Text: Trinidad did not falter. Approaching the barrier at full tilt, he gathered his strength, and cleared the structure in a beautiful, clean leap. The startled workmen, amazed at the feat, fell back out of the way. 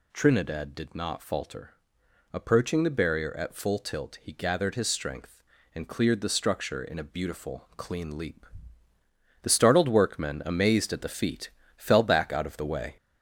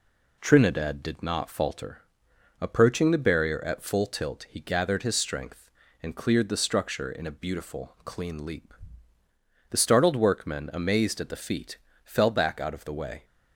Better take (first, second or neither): second